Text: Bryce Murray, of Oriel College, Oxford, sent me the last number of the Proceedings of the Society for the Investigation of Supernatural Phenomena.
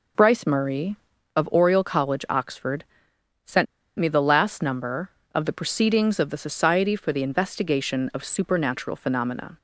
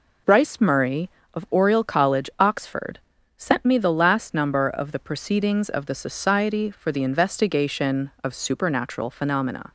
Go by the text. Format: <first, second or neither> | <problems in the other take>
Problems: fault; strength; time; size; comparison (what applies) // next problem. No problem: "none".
second | pauses between "sent" and "me"; slight; at 3.6 s; 0.33 s long